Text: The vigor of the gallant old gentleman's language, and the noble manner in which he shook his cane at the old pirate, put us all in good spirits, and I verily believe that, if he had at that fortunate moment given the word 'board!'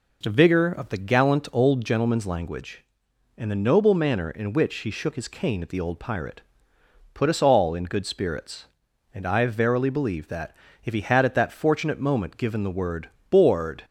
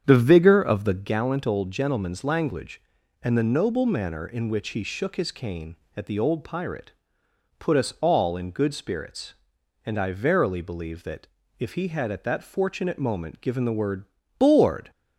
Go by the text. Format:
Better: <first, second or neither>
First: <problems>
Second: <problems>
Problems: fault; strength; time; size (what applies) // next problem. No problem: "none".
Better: first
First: pauses between "word" and "board"; slight; at 13.0 s; 0.24 s long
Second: starts louder than the rest; strong; until 1.2 s; 8 dB // pauses between "word" and "board"; slight; at 14.0 s; 0.36 s long